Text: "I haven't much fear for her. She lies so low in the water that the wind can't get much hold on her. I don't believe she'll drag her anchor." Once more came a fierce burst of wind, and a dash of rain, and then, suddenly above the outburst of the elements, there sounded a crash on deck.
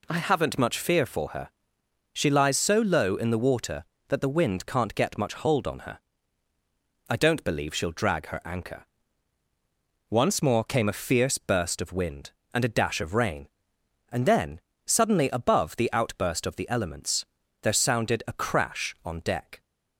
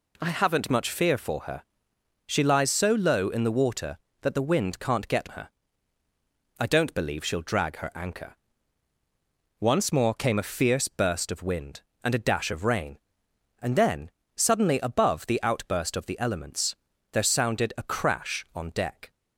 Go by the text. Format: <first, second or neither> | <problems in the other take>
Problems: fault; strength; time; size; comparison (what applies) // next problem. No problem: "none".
first | skips "much hold on"; at 5.2 s